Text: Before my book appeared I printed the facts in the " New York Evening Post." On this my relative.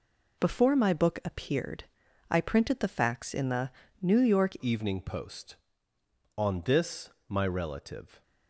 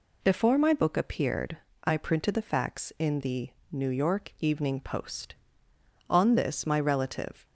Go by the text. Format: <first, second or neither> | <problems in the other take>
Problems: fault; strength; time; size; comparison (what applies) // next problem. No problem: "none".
second | pauses between "appeared" and "I"; noticeable; at 1.8 s; 0.46 s long; slight in the second // changes voice at "Evening"; from 4.6 s on; 3.6 s long // pauses between "this" and "my"; slight; at 7.1 s; 0.18 s long